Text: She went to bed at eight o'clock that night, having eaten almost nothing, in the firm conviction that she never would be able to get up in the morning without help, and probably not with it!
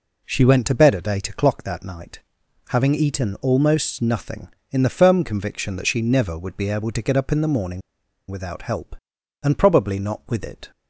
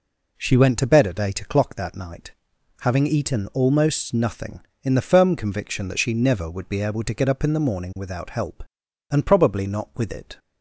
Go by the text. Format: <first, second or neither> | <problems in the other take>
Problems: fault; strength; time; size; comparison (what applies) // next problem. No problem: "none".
second | pauses between "morning" and "without"; noticeable; at 7.8 s; 0.49 s long